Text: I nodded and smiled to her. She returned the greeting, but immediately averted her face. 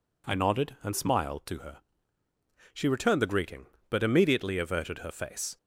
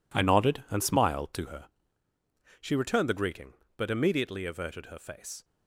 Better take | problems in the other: first | gets quieter; strong; throughout; 12 dB

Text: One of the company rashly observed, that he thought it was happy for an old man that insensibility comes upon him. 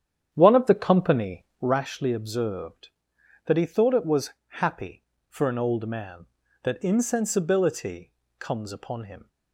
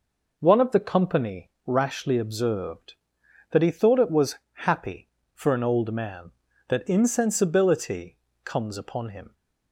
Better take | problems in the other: second | starts louder than the rest; strong; until 1.8 s; 9 dB // pauses between "company" and "rashly"; slight; at 1.4 s; 0.16 s long; slight in the second // pauses between "was" and "happy"; slight; at 4.3 s; 0.16 s long; slight in the second // pauses between "insensibility" and "comes"; slight; at 8.1 s; 0.28 s long; slight in the second

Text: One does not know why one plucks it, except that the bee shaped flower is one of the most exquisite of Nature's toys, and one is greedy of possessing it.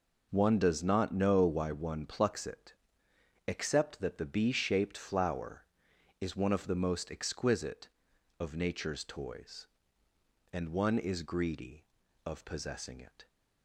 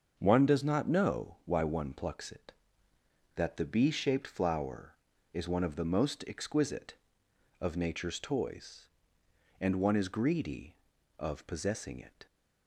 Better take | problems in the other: first | starts louder than the rest; until 1.1 s; 6.5 dB // skips "except"; at 2.9 s

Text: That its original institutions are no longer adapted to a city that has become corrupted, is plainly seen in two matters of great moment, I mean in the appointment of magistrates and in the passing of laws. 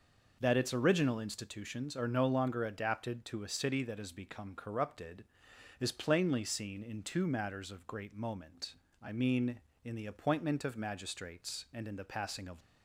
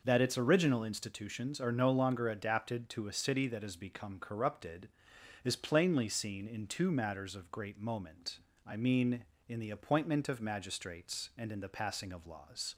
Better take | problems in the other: second | stops before "laws"; at 12.6 s

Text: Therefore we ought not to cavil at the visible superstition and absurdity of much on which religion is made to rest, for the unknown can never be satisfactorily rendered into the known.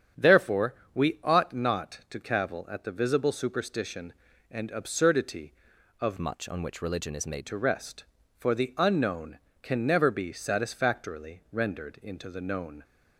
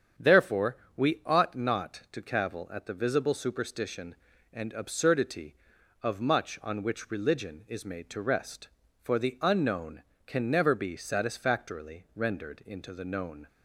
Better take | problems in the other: second | starts louder than the rest; strong; until 1.4 s; 8.5 dB; strong in the second // pauses between "Therefore" and "we"; slight; at 0.7 s; 0.18 s long; slight in the second // changes voice from "much" to "made"; from 6.1 to 7.4 s; 1.3 s long

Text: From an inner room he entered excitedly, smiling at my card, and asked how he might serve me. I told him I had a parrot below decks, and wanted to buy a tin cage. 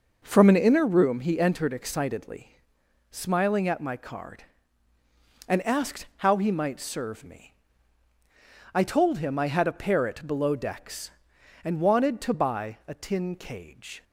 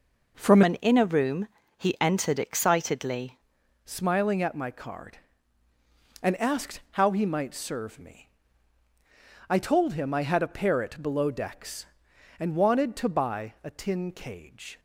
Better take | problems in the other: first | changes voice from "an" to "excitedly"; from 0.6 to 3.3 s; 2.7 s long // pauses between "room" and "he"; slight; at 1.4 s; 0.28 s long

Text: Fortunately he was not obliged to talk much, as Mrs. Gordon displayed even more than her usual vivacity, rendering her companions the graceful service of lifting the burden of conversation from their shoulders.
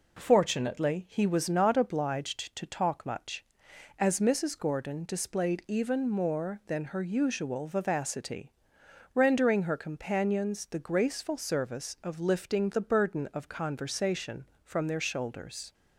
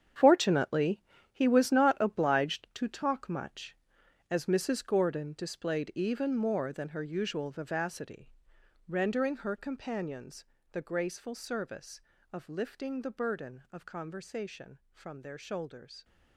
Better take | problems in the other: first | gets quieter; strong; throughout; 12.5 dB // pauses between "Fortunately" and "he"; slight; at 0.9 s; 0.32 s long // pauses between "companions" and "the"; slight; at 10.4 s; 0.28 s long

